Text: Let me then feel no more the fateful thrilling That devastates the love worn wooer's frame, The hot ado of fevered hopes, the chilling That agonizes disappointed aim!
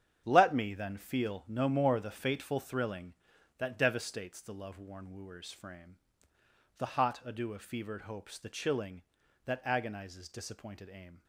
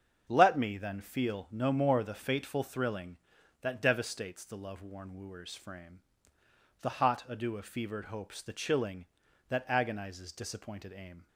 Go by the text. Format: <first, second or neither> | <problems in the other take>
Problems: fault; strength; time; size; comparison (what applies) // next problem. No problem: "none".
second | gets quieter; strong; throughout; 10.5 dB // starts louder than the rest; strong; until 1.2 s; 8.5 dB; also in the second